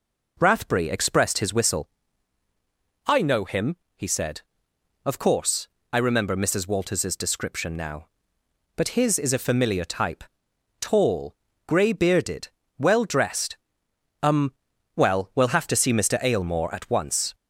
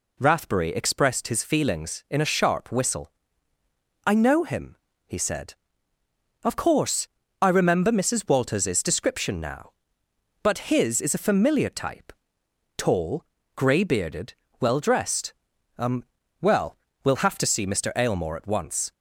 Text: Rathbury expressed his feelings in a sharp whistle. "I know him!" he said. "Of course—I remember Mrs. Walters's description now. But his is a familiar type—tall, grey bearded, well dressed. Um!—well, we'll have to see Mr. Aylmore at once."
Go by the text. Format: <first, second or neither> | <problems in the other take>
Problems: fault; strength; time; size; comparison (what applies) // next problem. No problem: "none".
second | skips "feelings in a sharp"; at 1.5 s